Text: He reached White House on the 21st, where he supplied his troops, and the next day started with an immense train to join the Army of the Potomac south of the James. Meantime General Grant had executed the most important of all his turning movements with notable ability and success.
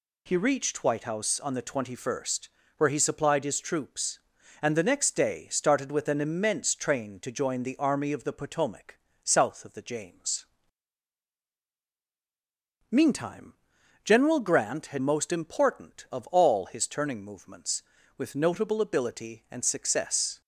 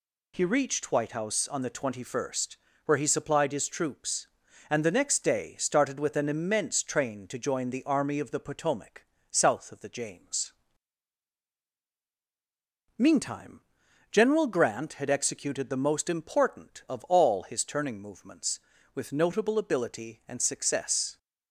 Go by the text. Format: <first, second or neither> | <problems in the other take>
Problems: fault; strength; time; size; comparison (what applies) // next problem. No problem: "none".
second | pauses between "Potomac" and "south"; slight; at 8.9 s; 0.24 s long; slight in the second // pauses between "Meantime" and "General"; noticeable; at 13.5 s; 0.50 s long; noticeable in the second // skips "executed the"; at 14.9 s